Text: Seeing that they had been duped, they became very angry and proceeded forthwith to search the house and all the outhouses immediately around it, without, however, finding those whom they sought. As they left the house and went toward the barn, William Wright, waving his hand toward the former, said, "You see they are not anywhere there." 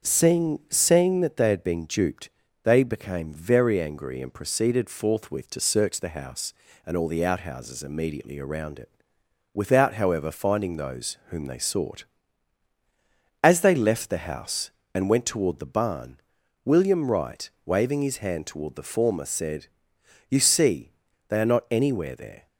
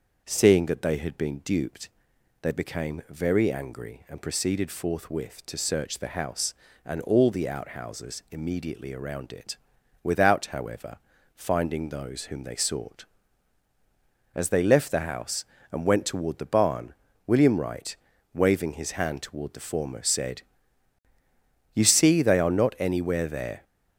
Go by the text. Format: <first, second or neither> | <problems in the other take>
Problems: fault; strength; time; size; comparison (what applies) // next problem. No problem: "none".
second | starts louder than the rest; until 1.1 s; 7 dB; also in the second // says "Seeing" twice; at 0.6 s // pauses between "see" and "they"; at 20.9 s; 0.38 s long